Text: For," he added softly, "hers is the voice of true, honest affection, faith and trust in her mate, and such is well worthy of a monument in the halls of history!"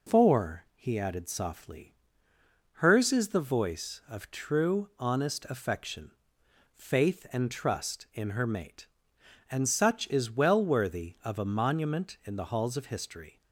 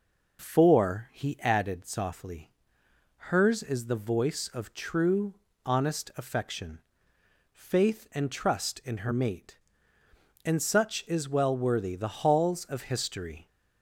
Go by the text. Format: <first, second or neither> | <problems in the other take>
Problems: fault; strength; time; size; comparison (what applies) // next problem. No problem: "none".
first | skips "of a monument in"; at 11.9 s